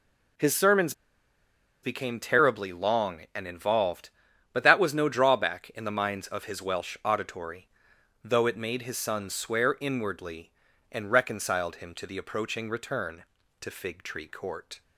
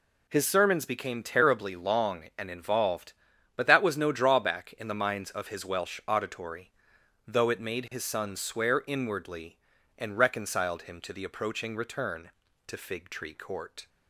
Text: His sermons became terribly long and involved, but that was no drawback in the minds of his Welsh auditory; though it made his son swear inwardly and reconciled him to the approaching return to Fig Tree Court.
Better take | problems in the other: second | pauses between "sermons" and "became"; noticeable; at 0.9 s; 0.91 s long

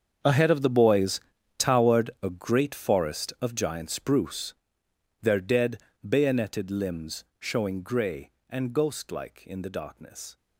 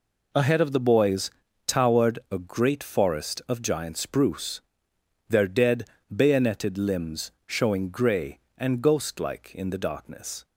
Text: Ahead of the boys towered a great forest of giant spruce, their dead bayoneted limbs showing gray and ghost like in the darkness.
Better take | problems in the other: second | gets quieter; strong; throughout; 16.5 dB // pauses between "boys" and "towered"; at 1.1 s; 0.38 s long; also in the second // pauses between "dead" and "bayoneted"; slight; at 5.7 s; 0.28 s long; slight in the second // pauses between "limbs" and "showing"; slight; at 7.2 s; 0.16 s long; slight in the second

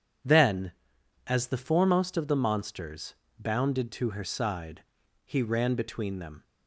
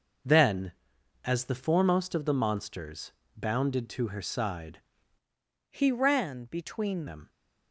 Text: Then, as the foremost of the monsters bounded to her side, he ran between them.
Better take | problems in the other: first | pauses between "monsters" and "bounded"; slight; at 3.1 s; 0.24 s long; slight in the first // changes voice from "he" to "between"; from 5.6 to 7.0 s; 1.4 s long

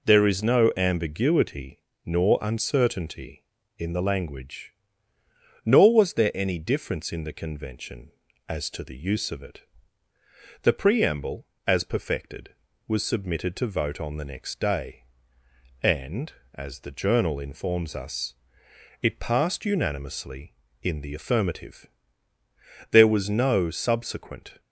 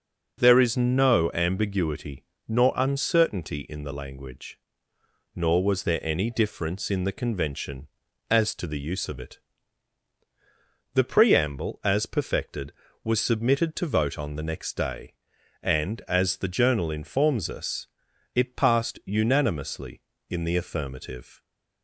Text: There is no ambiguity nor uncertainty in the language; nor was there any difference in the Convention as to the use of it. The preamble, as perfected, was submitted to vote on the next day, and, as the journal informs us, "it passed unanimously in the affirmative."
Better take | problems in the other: second | pauses between "ambiguity" and "nor"; slight; at 1.8 s; 0.24 s long; slight in the second // goes on to say "There was no subsequent"; strong; from 22.8 s on; 1.7 s long

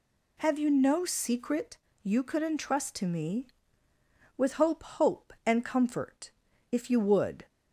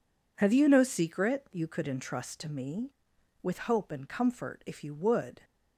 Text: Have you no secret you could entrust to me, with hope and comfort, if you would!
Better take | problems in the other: second | pauses between "secret" and "you"; slight; at 1.7 s; 0.26 s long // says "hope" twice; at 4.8 s

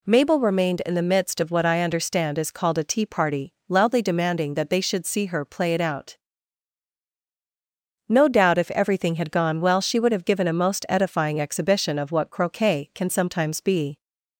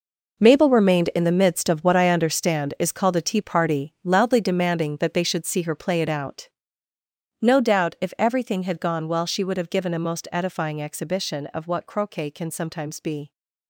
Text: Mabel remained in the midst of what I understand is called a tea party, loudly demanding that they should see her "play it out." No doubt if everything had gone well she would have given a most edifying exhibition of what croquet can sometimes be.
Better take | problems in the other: first | gets quieter; strong; throughout; 12 dB

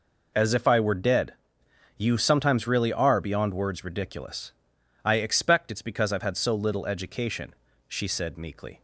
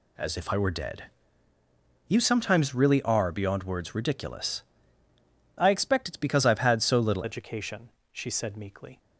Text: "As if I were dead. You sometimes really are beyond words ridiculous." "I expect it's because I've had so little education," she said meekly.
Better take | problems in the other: first | changes voice at "education"; from 7.2 s on; 1.7 s long

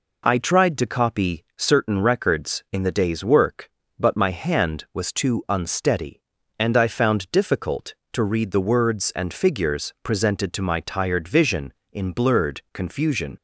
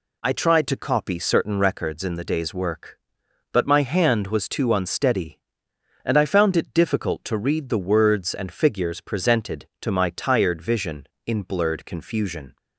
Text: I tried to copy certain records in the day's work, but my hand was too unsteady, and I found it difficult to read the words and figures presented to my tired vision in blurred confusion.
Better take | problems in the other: second | skips "it"; at 7.3 s

